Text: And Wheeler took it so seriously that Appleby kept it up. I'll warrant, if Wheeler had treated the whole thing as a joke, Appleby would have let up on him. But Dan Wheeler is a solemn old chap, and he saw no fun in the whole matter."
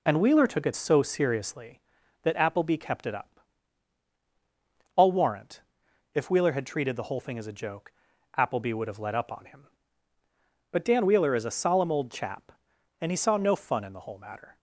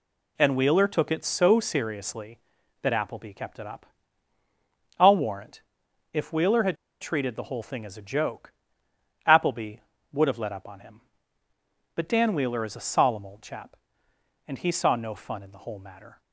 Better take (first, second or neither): first